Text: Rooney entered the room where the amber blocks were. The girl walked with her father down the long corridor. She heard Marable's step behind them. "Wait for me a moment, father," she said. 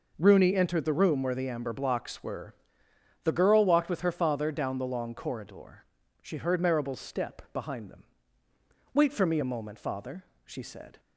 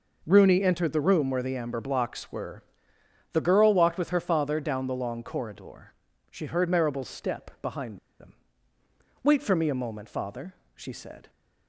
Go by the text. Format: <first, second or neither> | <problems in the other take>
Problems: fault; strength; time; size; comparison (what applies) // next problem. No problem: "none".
first | pauses between "behind" and "them"; slight; at 7.9 s; 0.20 s long